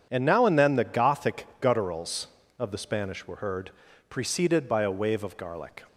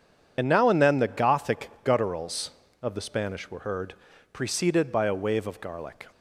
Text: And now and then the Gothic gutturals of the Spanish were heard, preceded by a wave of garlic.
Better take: first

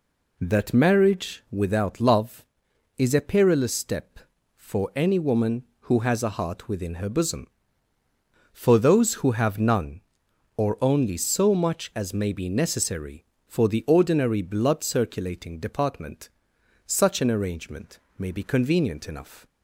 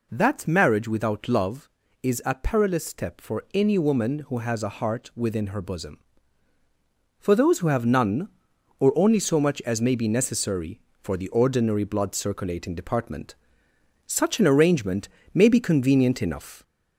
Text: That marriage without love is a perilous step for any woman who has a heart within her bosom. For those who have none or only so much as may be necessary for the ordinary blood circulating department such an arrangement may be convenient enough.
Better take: first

